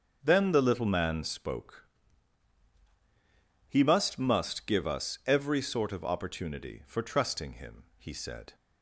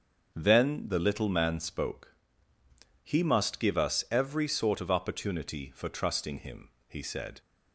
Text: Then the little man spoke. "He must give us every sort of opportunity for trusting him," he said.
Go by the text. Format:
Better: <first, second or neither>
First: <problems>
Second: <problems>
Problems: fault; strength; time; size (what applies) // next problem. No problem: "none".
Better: second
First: starts louder than the rest; until 1.2 s; 6.5 dB // says "must" twice; at 4.1 s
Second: starts louder than the rest; until 1.3 s; 6.5 dB